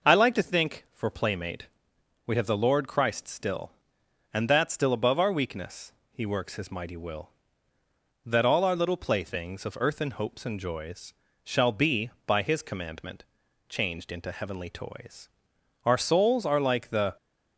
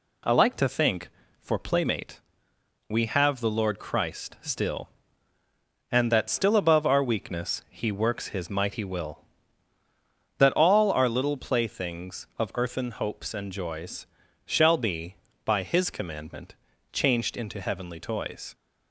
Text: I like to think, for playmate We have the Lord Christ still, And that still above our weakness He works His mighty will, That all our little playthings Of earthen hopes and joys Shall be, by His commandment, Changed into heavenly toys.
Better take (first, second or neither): second